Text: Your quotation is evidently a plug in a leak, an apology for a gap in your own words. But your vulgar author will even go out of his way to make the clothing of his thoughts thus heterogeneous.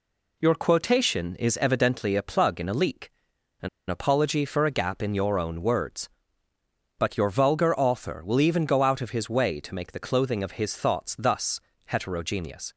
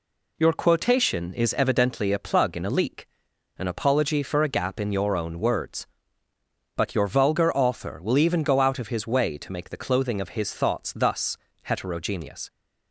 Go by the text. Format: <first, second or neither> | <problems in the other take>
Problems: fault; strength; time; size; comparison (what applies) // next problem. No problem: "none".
second | pauses between "an" and "apology"; slight; at 3.6 s; 0.21 s long // pauses between "thus" and "heterogeneous"; slight; at 11.6 s; 0.24 s long; slight in the second